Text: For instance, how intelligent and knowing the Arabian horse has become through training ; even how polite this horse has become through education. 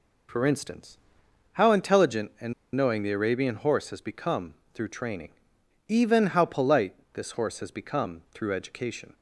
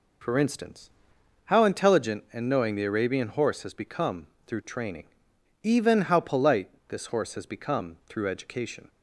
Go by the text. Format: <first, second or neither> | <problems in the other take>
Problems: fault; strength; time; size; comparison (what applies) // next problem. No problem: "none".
second | pauses between "and" and "knowing"; slight; at 2.5 s; 0.22 s long // pauses between "become" and "through"; slight; at 4.5 s; 0.18 s long; slight in the second // pauses between "polite" and "this"; slight; at 6.9 s; 0.18 s long; slight in the second